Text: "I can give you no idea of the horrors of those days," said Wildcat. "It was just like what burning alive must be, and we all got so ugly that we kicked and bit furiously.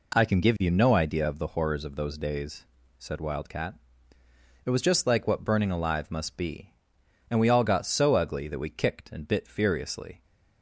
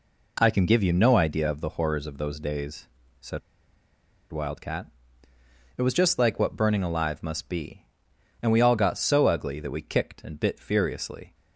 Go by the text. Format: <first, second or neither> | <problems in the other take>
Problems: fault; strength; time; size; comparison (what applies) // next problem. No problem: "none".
first | pauses between "said" and "Wildcat"; noticeable; at 3.4 s; 0.92 s long